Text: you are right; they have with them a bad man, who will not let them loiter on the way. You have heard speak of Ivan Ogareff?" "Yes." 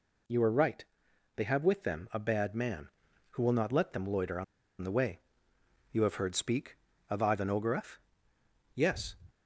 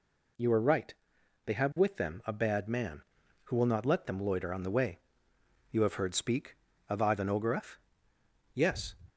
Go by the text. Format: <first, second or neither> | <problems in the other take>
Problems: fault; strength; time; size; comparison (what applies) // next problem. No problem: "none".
second | pauses between "on" and "the"; at 4.4 s; 0.37 s long